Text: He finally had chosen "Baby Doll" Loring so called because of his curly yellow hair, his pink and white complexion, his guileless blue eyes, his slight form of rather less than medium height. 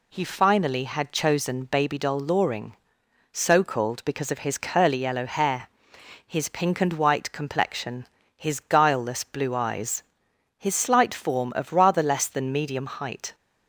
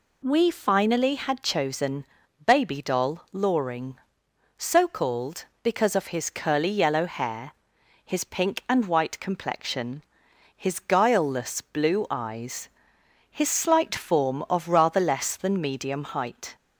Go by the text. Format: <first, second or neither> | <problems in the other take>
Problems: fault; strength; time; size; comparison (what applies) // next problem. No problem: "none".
first | says "We" for "He"; at 0.2 s // pauses between "chosen" and "Baby"; at 2.0 s; 0.40 s long